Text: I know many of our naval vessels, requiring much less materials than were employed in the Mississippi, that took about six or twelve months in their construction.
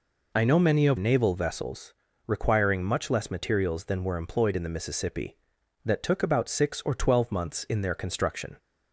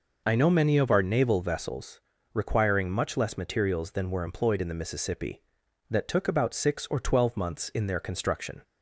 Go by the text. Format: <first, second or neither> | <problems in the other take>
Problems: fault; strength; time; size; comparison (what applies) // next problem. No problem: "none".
second | skips "our"; at 0.9 s